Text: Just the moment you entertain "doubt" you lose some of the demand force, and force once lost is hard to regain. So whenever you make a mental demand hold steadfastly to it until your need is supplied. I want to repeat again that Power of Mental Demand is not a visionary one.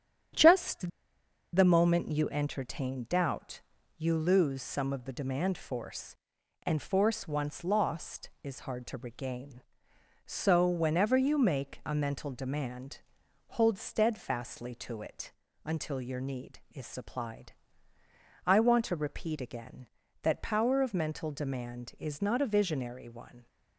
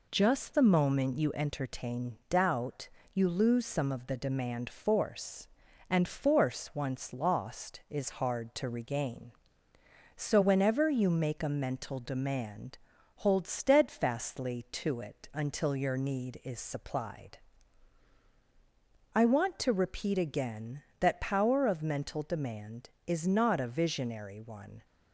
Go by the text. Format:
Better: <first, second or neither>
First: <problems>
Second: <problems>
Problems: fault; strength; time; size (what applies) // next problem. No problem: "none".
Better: second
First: starts louder than the rest; strong; until 2.0 s; 9 dB // pauses between "Just" and "the"; noticeable; at 0.8 s; 0.65 s long // pauses between "doubt" and "you"; at 3.6 s; 0.38 s long // pauses between "demand" and "hold"; at 13.0 s; 0.44 s long // pauses between "it" and "until"; slight; at 15.2 s; 0.34 s long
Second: pauses between "doubt" and "you"; slight; at 2.8 s; 0.24 s long // pauses between "demand" and "hold"; at 12.7 s; 0.42 s long